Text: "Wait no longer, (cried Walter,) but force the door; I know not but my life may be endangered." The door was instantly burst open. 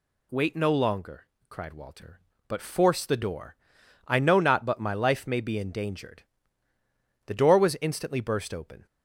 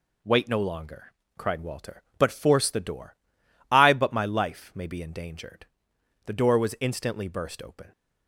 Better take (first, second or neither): first